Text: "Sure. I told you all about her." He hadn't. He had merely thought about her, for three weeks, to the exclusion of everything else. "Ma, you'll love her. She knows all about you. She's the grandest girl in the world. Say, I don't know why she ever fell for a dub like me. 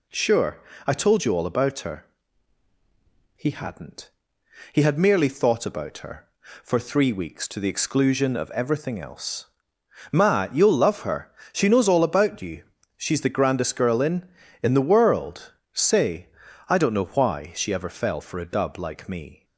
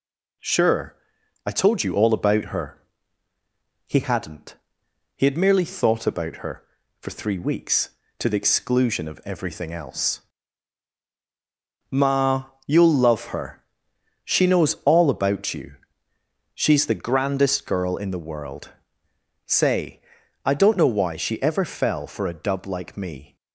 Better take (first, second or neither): second